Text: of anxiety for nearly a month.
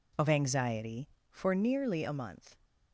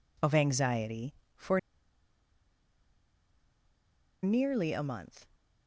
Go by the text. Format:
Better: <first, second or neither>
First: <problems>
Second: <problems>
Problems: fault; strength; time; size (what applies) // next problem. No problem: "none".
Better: first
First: none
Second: pauses between "for" and "nearly"; strong; at 1.5 s; 2.6 s long